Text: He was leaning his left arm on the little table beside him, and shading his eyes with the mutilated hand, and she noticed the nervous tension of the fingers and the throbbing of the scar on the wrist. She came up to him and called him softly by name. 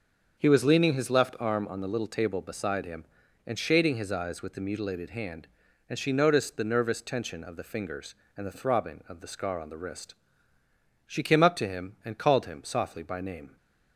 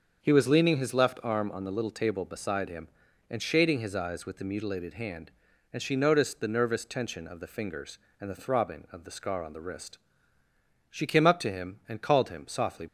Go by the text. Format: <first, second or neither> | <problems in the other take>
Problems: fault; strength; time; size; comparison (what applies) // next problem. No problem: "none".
first | starts louder than the rest; until 1.2 s; 6.5 dB; also in the first // stops before "by name"; at 12.8 s